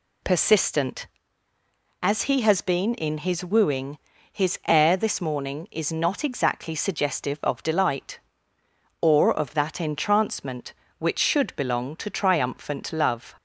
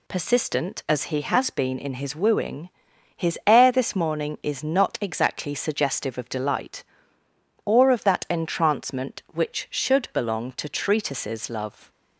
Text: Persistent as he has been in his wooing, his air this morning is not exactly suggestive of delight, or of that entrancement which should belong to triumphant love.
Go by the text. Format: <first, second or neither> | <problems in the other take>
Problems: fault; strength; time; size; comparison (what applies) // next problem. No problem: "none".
first | says "treatises" for "triumphant"; at 10.6 s